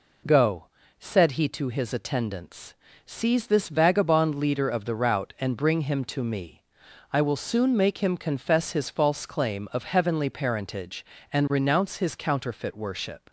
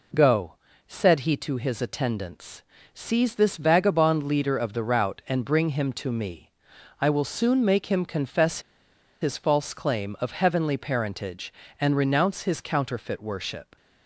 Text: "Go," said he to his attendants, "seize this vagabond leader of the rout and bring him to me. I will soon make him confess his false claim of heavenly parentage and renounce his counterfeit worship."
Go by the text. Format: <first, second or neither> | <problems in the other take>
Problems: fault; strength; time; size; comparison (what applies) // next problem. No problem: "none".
first | pauses between "confess" and "his"; noticeable; at 8.6 s; 0.61 s long